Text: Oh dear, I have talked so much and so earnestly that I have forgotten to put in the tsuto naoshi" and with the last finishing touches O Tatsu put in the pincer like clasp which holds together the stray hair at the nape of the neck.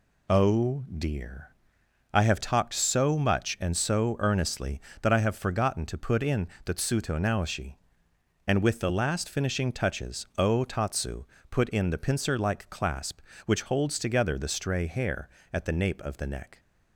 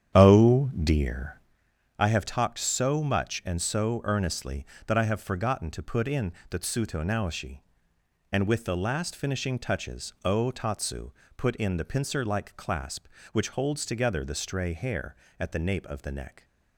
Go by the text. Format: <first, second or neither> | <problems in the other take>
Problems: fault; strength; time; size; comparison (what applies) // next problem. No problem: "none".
first | starts louder than the rest; strong; until 1.5 s; 9.5 dB // pauses between "in" and "the"; slight; at 6.3 s; 0.16 s long; slight in the first // pauses between "Tatsu" and "put"; slight; at 11.1 s; 0.26 s long; slight in the first